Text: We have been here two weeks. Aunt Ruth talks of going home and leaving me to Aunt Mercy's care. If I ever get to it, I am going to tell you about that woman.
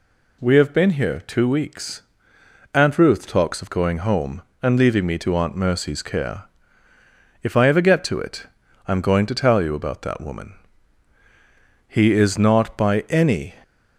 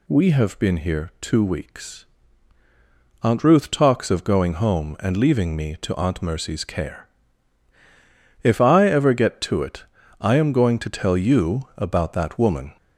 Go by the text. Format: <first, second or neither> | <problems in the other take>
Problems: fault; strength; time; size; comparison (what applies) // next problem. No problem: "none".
second | goes on to say "He is not by any"; from 11.8 s on; 1.6 s long